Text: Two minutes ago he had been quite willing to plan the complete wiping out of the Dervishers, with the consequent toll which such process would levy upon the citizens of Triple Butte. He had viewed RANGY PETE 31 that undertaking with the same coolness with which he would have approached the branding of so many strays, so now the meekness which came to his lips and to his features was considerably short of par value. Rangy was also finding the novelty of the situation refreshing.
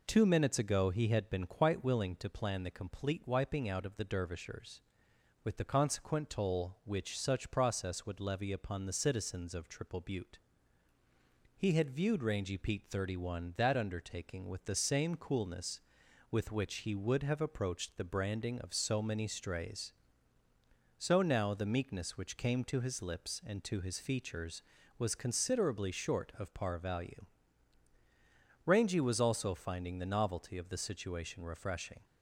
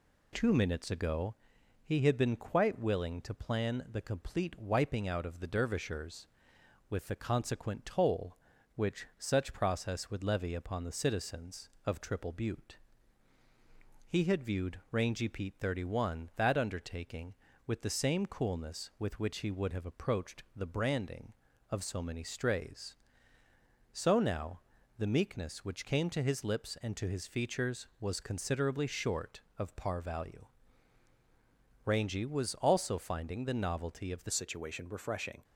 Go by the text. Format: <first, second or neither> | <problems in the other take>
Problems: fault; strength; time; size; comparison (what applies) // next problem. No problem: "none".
first | pauses between "ago" and "he"; noticeable; at 1.3 s; 0.50 s long // pauses between "now" and "the"; at 24.5 s; 0.38 s long // changes voice at "situation"; from 34.3 s on; 1.1 s long